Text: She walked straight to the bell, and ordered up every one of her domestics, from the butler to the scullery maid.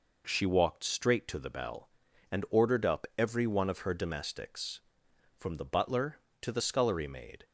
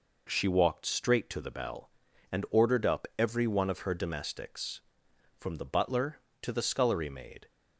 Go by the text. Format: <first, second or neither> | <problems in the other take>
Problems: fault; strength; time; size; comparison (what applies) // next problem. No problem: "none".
neither | none